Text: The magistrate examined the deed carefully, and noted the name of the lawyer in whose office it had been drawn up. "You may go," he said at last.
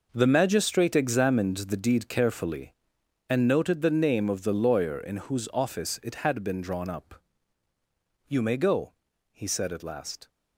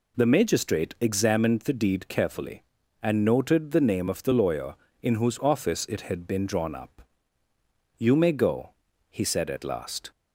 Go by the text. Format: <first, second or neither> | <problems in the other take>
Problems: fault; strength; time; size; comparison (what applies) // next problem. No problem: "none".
second | gets quieter; strong; throughout; 13.5 dB